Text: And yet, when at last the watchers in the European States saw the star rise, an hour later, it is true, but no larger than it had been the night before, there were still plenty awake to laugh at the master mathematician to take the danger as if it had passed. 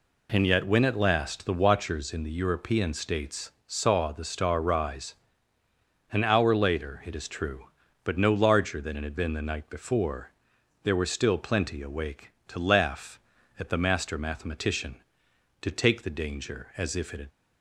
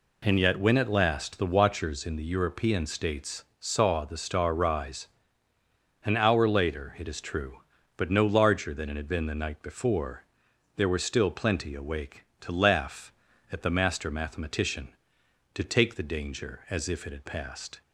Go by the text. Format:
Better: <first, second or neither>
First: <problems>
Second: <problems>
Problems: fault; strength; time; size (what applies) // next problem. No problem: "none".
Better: second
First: pauses between "States" and "saw"; slight; at 3.5 s; 0.16 s long // stops before "passed"; at 17.3 s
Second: pauses between "States" and "saw"; slight; at 3.4 s; 0.16 s long